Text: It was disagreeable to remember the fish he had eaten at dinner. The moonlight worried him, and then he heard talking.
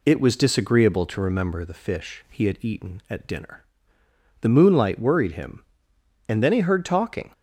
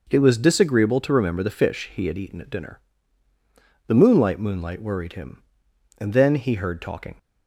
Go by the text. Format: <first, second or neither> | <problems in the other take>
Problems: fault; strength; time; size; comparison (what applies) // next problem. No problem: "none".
first | says "moonlight" twice; at 4.3 s